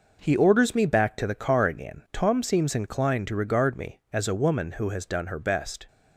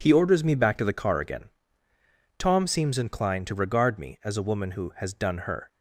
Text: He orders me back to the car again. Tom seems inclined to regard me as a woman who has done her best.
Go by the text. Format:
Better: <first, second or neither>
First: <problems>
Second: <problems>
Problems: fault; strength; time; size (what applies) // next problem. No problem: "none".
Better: first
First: none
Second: stops before "best"; at 5.6 s